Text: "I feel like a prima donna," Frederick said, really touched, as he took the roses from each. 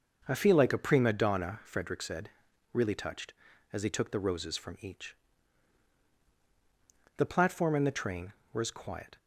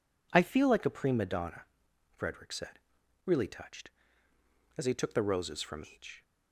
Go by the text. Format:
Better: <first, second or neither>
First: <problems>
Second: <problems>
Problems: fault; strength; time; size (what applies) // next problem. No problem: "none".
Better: second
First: goes on to say "The platform and the train were as quiet"; strong; from 7.1 s on; 2.0 s long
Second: none